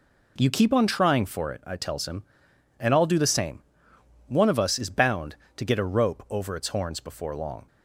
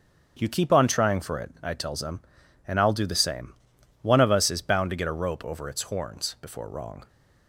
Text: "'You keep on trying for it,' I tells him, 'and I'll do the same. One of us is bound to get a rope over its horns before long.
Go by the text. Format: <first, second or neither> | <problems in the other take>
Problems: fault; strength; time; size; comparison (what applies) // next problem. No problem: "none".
first | starts louder than the rest; strong; until 1.4 s; 7 dB // says "wrong" for "long"; at 6.6 s